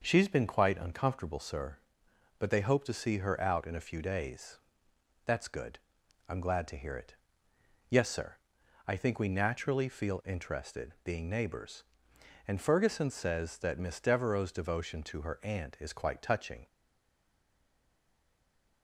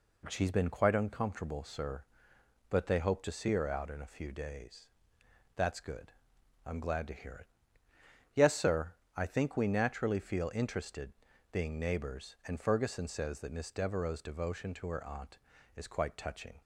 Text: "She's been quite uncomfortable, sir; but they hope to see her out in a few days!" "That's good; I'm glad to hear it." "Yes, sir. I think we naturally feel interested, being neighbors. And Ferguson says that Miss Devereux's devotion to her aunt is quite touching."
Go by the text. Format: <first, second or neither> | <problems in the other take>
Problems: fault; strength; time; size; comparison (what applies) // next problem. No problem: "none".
second | stays silent after the last word; from 16.6 s on; 2.2 s long